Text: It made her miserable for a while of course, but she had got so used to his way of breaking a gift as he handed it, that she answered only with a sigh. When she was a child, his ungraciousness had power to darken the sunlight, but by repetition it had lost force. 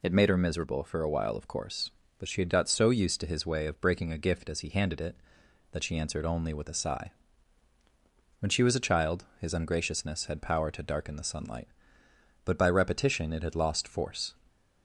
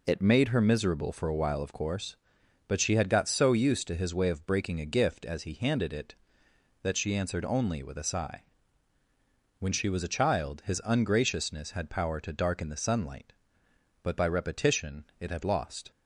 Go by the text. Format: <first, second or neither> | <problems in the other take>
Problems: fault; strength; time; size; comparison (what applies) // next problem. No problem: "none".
first | stops before "force"; at 15.9 s